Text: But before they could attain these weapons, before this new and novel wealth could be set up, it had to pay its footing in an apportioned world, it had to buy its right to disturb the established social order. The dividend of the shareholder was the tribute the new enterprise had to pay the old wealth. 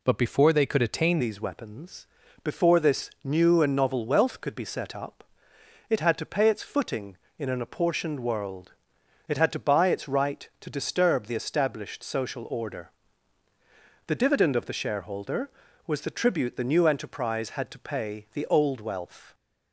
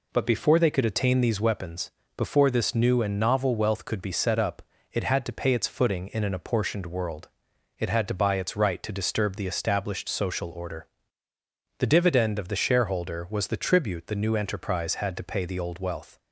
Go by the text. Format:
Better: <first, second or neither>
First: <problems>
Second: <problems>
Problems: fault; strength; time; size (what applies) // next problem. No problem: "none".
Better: second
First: changes voice at "these"; from 1.2 s on; 18.1 s long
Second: none